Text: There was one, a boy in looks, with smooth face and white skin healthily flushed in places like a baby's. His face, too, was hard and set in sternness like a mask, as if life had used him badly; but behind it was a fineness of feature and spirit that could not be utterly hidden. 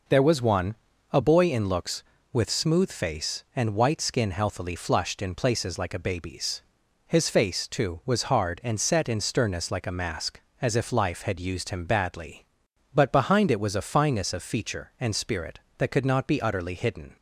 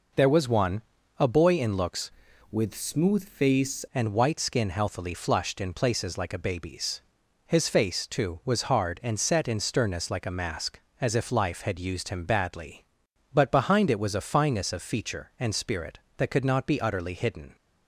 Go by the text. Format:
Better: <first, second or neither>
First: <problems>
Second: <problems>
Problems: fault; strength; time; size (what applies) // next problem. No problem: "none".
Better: first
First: none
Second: changes voice from "with" to "face"; from 2.5 to 3.8 s; 1.3 s long